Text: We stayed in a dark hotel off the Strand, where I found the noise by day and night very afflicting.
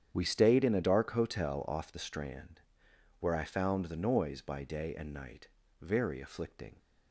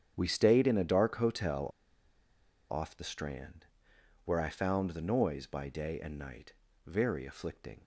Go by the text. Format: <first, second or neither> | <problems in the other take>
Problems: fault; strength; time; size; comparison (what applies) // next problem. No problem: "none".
first | starts louder than the rest; strong; until 1.1 s; 9 dB; strong in the first // pauses between "hotel" and "off"; at 1.6 s; 1.0 s long // pauses between "night" and "very"; slight; at 6.5 s; 0.34 s long; slight in the first